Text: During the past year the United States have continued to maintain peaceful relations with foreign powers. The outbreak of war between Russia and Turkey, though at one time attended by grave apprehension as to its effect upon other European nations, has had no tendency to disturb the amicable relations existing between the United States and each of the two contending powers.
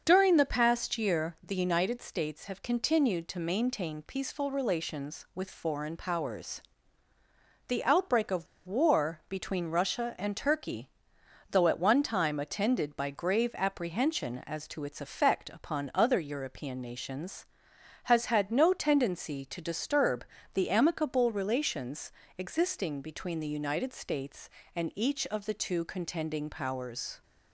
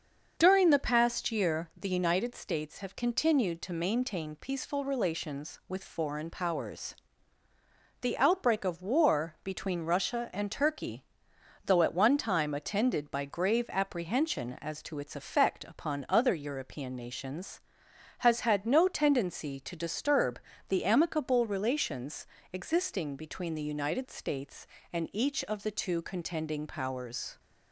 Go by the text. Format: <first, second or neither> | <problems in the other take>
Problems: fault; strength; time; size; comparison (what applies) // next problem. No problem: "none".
second | starts louder than the rest; until 1.0 s; 6.5 dB; also in the second // pauses between "of" and "war"; slight; at 8.4 s; 0.21 s long // pauses between "disturb" and "the"; slight; at 20.2 s; 0.30 s long; slight in the second // pauses between "relations" and "existing"; slight; at 22.1 s; 0.26 s long; slight in the second